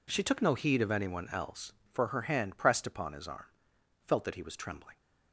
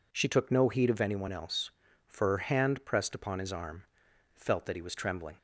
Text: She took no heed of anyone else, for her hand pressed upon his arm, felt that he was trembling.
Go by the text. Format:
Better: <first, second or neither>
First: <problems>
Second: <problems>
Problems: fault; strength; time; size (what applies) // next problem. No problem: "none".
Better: neither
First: none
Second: none